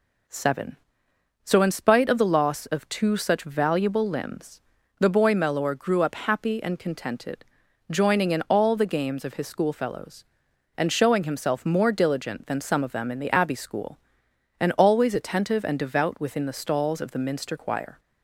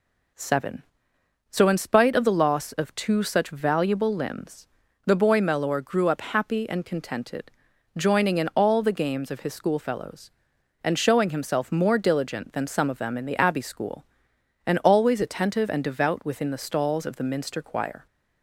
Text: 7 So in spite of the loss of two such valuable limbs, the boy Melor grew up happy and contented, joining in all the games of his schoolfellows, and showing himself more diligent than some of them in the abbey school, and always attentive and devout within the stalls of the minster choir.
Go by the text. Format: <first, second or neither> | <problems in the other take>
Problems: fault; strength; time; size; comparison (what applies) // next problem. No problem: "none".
neither | none